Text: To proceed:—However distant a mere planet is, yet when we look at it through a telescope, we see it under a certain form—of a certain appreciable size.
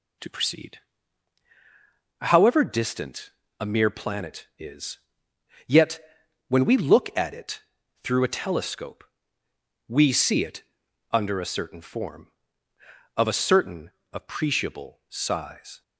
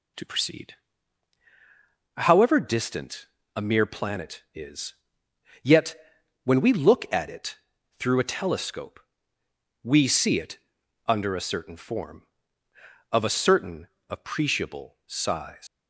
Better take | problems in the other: first | pauses between "distant" and "a"; slight; at 3.2 s; 0.30 s long; slight in the first // pauses between "yet" and "when"; noticeable; at 5.9 s; 0.48 s long; noticeable in the first // pauses between "it" and "through"; at 7.5 s; 0.40 s long; also in the first // pauses between "it" and "under"; noticeable; at 10.5 s; 0.50 s long; noticeable in the first // pauses between "certain" and "appreciable"; slight; at 13.8 s; 0.20 s long; slight in the first // leaves "size" unfinished; at 15.6 s; 125 ms

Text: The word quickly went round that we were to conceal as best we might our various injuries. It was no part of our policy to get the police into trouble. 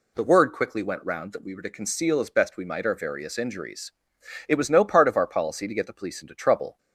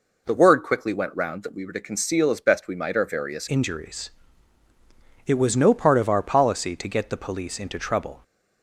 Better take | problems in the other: first | changes voice at "injuries"; from 3.4 s on; 4.8 s long

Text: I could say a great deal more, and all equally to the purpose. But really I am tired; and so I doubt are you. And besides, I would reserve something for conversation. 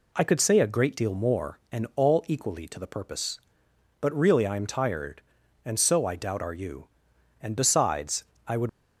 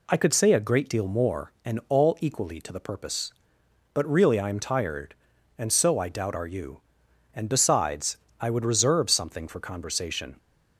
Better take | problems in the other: second | stops before "reserve something for conversation"; at 8.6 s

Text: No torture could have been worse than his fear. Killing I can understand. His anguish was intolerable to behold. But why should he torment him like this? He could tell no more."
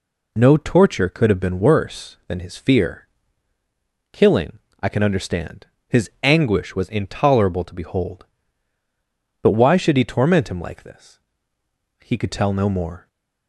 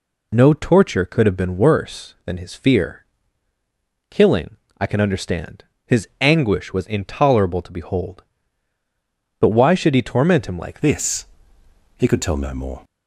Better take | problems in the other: first | pauses between "Killing" and "I"; slight; at 4.5 s; 0.22 s long; slight in the first // changes voice at "this"; from 10.8 s on; 2.0 s long

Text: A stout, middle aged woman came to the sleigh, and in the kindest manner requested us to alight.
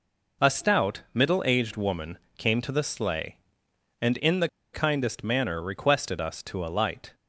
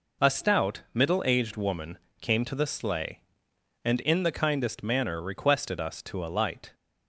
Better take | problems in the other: second | pauses between "woman" and "came"; slight; at 2.1 s; 0.20 s long; slight in the second // pauses between "the" and "kindest"; slight; at 4.4 s; 0.26 s long

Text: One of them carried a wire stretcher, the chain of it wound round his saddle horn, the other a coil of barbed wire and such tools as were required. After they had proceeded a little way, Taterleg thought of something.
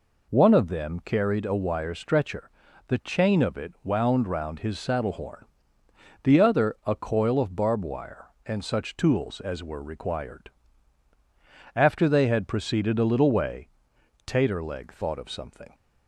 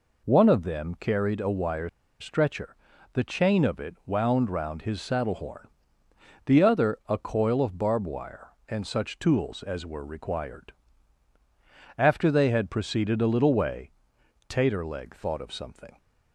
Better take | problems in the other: first | pauses between "wire" and "stretcher"; slight; at 1.8 s; 0.31 s long

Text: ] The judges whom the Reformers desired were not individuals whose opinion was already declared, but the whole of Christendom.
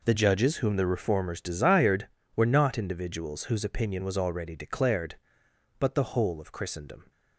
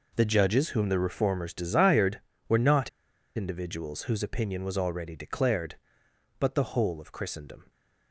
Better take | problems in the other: first | pauses between "not" and "individuals"; noticeable; at 2.8 s; 0.48 s long

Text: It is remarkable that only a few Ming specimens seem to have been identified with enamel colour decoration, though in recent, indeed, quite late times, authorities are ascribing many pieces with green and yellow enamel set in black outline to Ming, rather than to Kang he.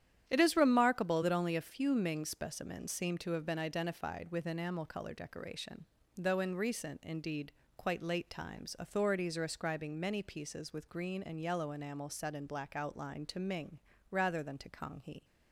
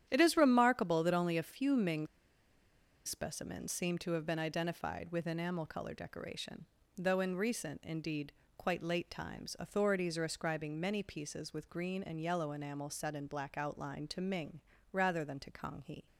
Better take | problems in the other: first | starts louder than the rest; strong; until 1.0 s; 10.5 dB; strong in the first // pauses between "Ming" and "specimens"; at 2.0 s; 0.99 s long

